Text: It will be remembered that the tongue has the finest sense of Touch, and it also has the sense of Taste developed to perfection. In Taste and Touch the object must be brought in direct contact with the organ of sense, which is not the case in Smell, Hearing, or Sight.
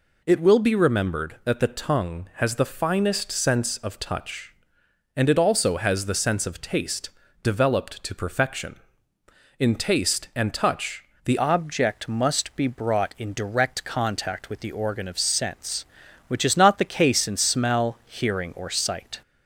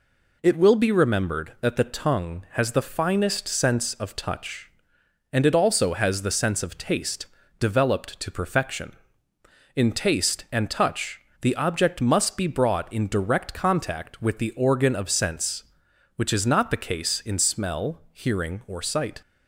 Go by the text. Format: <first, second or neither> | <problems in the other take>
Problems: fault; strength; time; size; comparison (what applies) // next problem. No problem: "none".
second | pauses between "Taste" and "developed"; slight; at 7.1 s; 0.32 s long; slight in the second // pauses between "Touch" and "the"; slight; at 11.0 s; 0.20 s long; slight in the second // changes voice at "object"; from 11.3 s on; 7.9 s long